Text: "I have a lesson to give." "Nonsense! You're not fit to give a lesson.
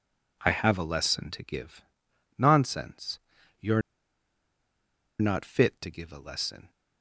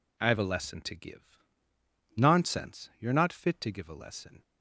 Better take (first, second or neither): second